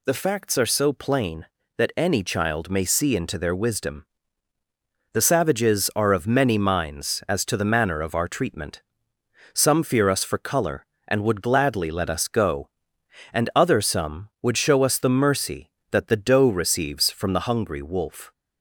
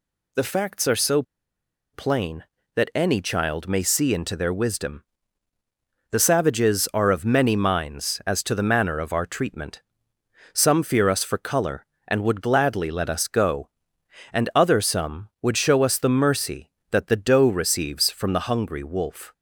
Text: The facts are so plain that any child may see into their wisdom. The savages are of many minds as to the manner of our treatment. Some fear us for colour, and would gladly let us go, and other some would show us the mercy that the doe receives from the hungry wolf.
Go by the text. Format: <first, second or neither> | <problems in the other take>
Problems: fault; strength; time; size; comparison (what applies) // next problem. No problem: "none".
first | pauses between "so" and "plain"; noticeable; at 1.2 s; 0.70 s long